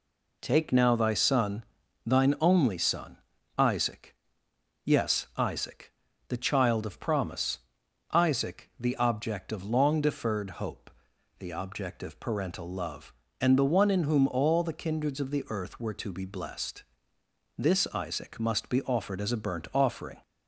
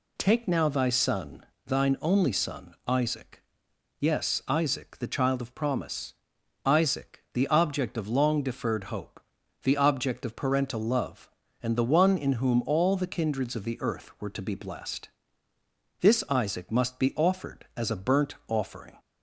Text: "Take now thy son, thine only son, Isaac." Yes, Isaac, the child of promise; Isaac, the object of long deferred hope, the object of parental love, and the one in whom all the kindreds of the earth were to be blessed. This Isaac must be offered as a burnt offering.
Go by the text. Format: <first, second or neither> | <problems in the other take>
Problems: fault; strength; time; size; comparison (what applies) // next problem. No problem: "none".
neither | none